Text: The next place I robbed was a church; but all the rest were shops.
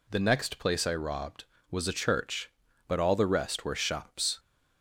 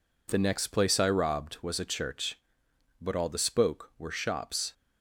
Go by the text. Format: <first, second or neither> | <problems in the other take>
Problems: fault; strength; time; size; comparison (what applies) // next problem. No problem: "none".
first | says "spoke" for "rest"; at 3.3 s